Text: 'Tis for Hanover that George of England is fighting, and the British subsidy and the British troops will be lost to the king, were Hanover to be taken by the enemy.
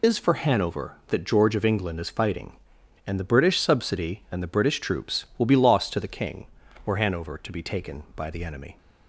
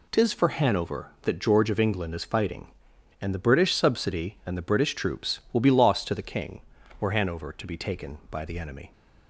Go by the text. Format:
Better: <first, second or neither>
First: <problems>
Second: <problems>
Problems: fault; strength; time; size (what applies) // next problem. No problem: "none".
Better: second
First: loses the start of "Tis"; at 0.0 s; 85 ms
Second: none